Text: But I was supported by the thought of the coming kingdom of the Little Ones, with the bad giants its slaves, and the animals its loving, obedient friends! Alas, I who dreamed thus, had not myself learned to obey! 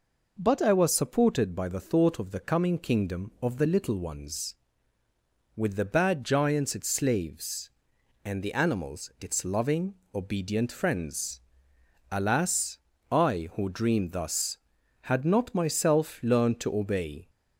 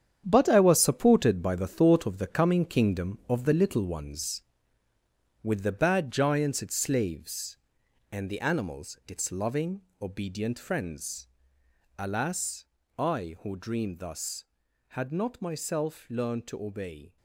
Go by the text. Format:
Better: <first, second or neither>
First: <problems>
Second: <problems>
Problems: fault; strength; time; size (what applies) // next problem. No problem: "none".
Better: first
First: none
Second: gets quieter; strong; throughout; 10.5 dB